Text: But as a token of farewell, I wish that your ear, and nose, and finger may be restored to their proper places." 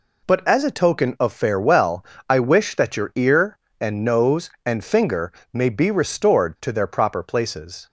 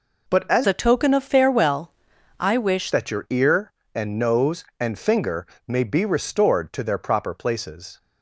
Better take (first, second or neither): first